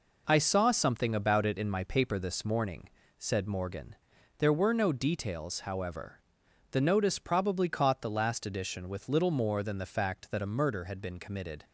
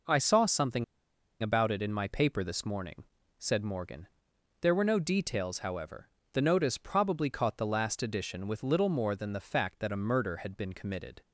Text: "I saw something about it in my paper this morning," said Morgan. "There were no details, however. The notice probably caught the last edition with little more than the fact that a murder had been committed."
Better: first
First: none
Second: pauses between "something" and "about"; noticeable; at 0.8 s; 0.56 s long

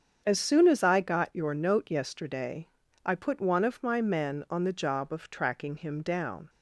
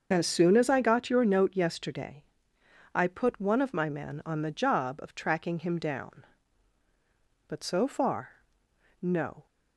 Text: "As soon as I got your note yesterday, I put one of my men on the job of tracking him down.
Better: first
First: starts louder than the rest; strong; until 1.2 s; 7.5 dB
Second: starts louder than the rest; until 1.1 s; 6.5 dB // goes on to say "But so far no"; strong; from 7.4 s on; 1.9 s long

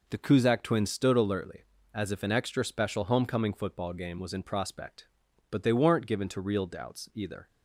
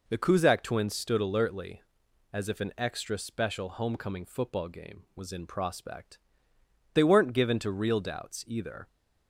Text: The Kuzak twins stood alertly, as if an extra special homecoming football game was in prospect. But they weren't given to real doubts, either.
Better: first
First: none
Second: skips "But"; at 6.5 s

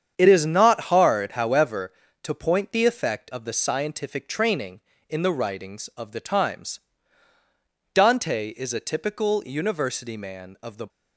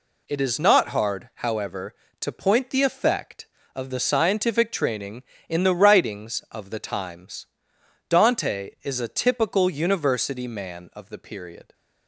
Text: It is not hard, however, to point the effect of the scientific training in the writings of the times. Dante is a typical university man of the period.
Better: second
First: starts louder than the rest; strong; until 1.1 s; 8 dB // stops before "period"; at 10.8 s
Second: none

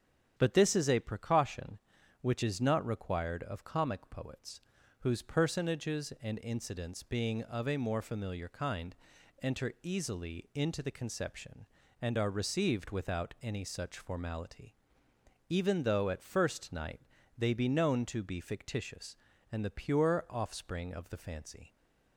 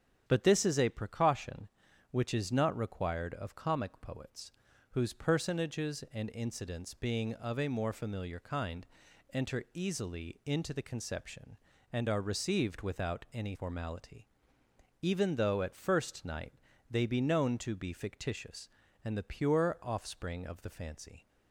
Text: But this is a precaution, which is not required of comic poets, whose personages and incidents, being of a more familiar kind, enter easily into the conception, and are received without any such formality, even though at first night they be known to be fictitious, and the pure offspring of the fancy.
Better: first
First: starts louder than the rest; strong; until 1.3 s; 9 dB // pauses between "night" and "they"; slight; at 17.0 s; 0.36 s long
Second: starts louder than the rest; strong; until 1.2 s; 8.5 dB // skips "such"; at 13.5 s // pauses between "night" and "they"; slight; at 16.5 s; 0.36 s long

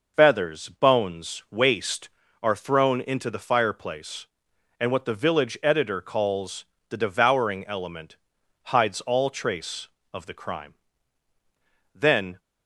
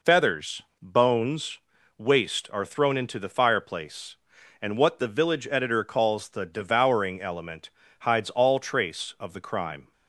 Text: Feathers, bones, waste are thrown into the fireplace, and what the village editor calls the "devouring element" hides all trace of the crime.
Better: second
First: pauses between "calls" and "the"; slight; at 6.6 s; 0.24 s long // pauses between "element" and "hides"; noticeable; at 8.1 s; 0.48 s long // goes on to say "Then"; slight; from 11.9 s on; 0.46 s long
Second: pauses between "element" and "hides"; slight; at 7.6 s; 0.30 s long

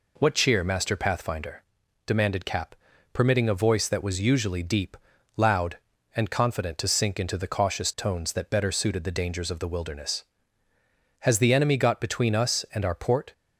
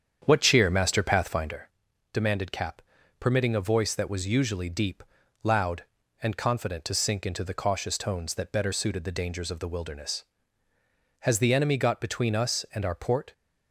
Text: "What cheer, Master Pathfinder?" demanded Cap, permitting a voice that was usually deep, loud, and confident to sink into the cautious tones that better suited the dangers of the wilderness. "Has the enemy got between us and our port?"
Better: first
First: none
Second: starts louder than the rest; strong; until 1.6 s; 8 dB

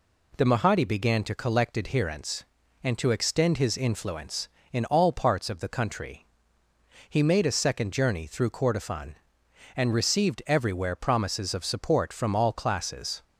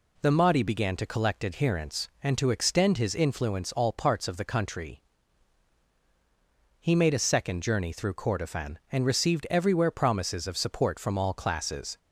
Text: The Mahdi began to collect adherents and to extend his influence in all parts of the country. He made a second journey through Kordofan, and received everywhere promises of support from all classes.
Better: first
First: none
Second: skips "in"; at 3.7 s

